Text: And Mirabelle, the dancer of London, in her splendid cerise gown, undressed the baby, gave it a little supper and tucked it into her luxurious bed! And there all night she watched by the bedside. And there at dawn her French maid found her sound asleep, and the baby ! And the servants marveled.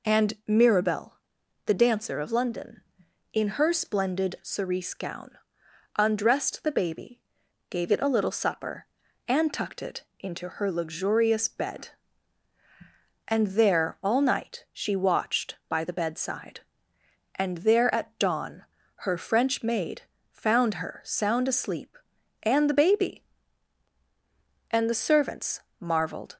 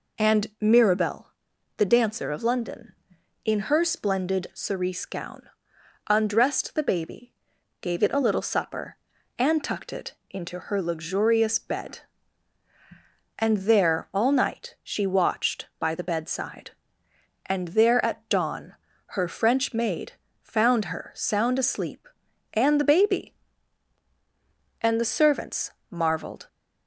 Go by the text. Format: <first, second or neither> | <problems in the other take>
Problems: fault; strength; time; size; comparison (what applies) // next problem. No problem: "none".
neither | pauses between "it" and "into"; slight; the same in both // pauses between "dawn" and "her"; slight; the same in both // pauses between "maid" and "found"; slight; the same in both // pauses between "servants" and "marveled"; slight; the same in both